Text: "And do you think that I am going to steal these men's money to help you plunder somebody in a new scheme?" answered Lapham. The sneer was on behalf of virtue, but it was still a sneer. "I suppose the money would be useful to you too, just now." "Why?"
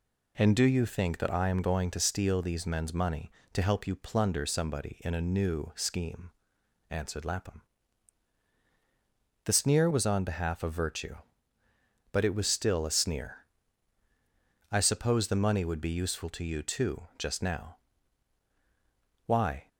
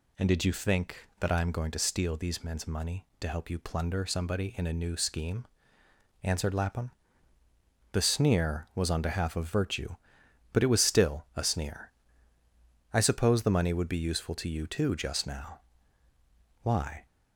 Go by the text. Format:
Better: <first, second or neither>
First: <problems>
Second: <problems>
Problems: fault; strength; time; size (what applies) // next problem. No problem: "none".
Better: first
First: none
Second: says "did" for "do"; at 0.2 s